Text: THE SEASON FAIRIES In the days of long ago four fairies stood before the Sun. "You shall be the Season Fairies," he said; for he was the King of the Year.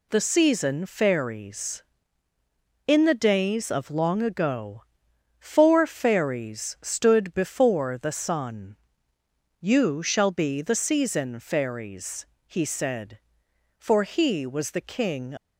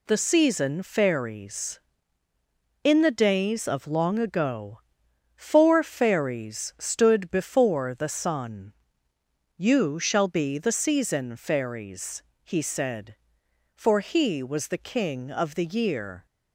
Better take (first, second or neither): second